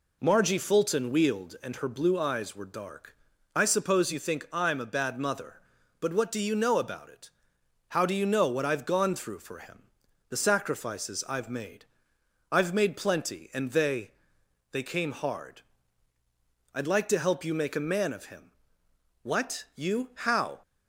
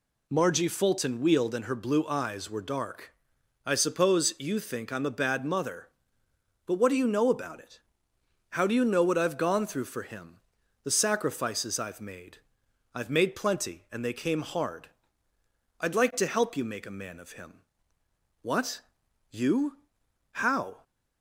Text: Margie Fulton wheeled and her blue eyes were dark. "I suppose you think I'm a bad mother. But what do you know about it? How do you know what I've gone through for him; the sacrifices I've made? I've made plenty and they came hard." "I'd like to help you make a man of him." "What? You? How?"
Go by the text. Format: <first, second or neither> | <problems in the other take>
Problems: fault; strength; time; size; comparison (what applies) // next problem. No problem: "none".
second | says "they" twice; at 14.7 s